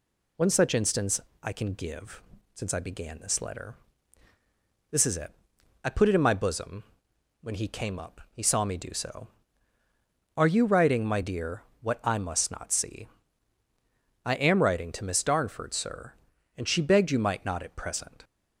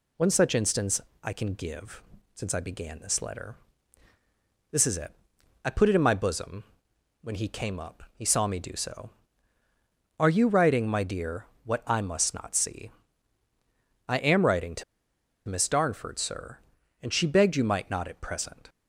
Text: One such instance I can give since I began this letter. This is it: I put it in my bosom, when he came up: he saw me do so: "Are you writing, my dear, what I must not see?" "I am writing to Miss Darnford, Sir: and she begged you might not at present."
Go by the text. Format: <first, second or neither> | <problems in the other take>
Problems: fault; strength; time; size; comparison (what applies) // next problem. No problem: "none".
first | pauses between "instance" and "I"; slight; at 1.0 s; 0.22 s long; slight in the first // pauses between "give" and "since"; slight; at 2.0 s; 0.32 s long; slight in the first // pauses between "to" and "Miss"; noticeable; at 14.8 s; 0.65 s long